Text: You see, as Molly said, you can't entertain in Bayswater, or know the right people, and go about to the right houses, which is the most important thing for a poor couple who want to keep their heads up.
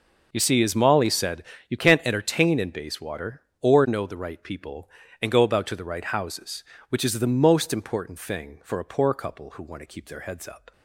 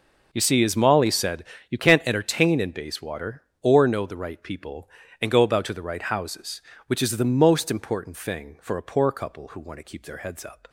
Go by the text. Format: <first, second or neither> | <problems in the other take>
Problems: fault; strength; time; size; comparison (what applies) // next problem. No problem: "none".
neither | none